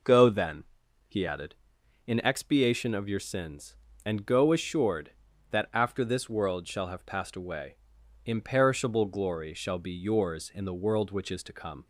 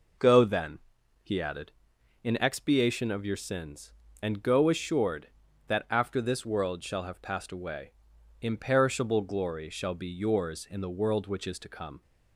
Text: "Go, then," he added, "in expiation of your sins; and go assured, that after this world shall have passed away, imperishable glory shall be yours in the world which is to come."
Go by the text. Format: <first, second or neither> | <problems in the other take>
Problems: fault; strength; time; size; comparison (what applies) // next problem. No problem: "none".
neither | none